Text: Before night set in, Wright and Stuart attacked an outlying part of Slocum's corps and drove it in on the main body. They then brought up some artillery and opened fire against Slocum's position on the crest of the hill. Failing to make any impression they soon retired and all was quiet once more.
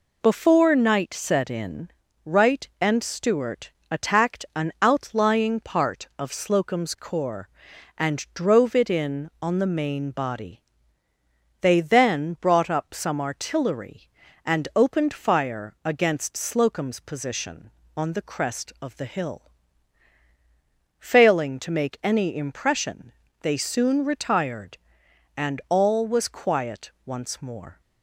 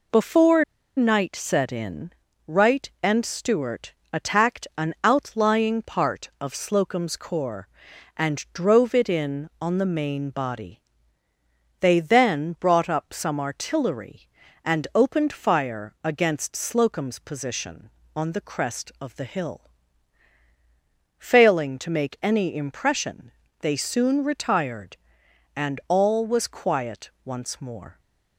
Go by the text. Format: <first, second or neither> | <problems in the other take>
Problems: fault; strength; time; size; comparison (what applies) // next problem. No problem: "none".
first | pauses between "Before" and "night"; slight; at 0.6 s; 0.32 s long // pauses between "Stuart" and "attacked"; slight; at 3.9 s; 0.20 s long; slight in the first // pauses between "impression" and "they"; slight; at 23.3 s; 0.30 s long; slight in the first